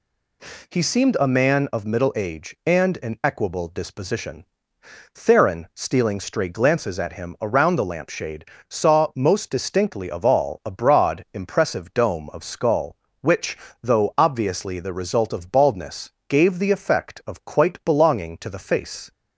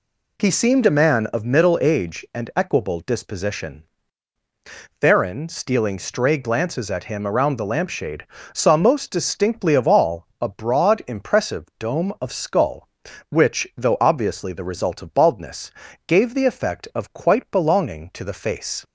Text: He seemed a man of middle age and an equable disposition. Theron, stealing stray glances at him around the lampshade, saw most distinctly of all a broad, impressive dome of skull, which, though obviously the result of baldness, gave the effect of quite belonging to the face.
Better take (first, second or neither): first